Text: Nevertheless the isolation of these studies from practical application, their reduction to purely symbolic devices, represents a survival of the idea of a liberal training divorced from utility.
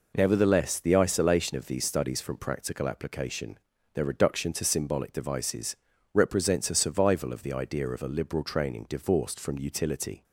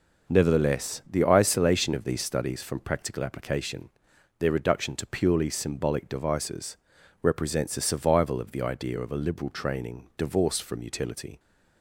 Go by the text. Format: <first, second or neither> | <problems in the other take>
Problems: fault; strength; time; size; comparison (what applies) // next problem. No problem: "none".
second | skips "purely"; at 4.6 s